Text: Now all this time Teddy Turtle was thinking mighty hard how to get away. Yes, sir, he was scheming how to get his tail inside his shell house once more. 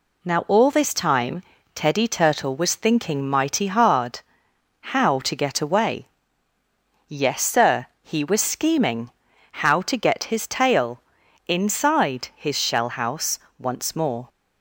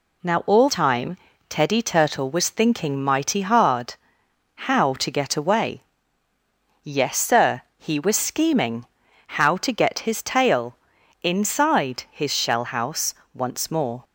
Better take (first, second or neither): first